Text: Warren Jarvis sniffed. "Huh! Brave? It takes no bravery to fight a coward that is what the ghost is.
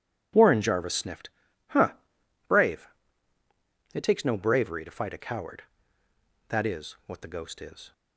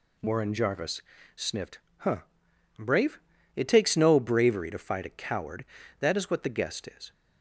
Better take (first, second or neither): first